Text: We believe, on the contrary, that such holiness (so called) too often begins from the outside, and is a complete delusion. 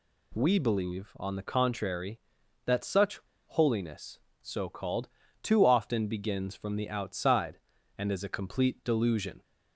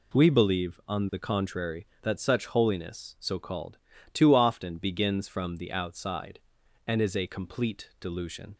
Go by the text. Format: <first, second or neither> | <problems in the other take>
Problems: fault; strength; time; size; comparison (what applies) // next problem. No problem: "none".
second | pauses between "such" and "holiness"; slight; at 3.1 s; 0.27 s long